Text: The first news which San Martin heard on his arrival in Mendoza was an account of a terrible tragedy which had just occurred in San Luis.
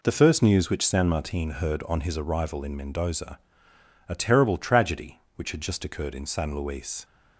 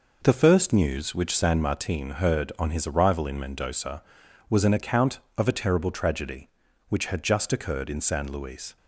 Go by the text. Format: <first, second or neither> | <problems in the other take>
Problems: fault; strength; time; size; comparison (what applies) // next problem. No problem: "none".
second | skips "was an account of"; at 3.7 s